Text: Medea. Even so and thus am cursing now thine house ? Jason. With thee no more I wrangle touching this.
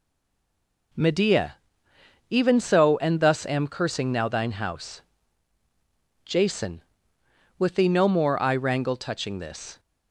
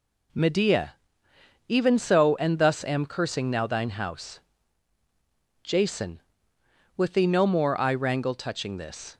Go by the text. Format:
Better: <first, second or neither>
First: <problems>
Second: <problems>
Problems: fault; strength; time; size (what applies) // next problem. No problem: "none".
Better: second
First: stays silent before the first word; slight; until 0.9 s; 0.9 s long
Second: none